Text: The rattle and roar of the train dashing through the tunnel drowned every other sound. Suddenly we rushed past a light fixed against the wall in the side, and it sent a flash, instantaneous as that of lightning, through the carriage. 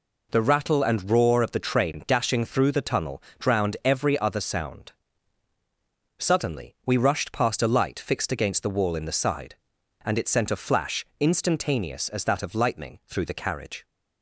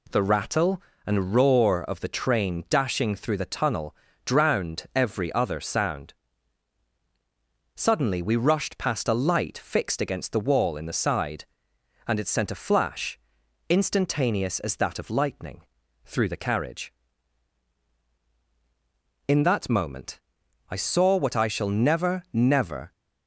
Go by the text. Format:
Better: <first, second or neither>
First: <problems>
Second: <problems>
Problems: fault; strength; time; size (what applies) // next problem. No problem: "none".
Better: first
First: pauses between "tunnel" and "drowned"; slight; at 3.2 s; 0.20 s long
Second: pauses between "tunnel" and "drowned"; slight; at 3.9 s; 0.30 s long // goes on to say "In that moment I saw what I shall never never"; strong; from 19.2 s on; 3.6 s long